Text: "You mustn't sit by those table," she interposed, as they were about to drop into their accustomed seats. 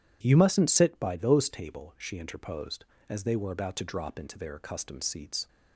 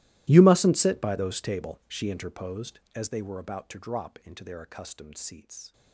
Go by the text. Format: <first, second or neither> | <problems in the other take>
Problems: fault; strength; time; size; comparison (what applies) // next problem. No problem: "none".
first | gets quieter; strong; throughout; 23 dB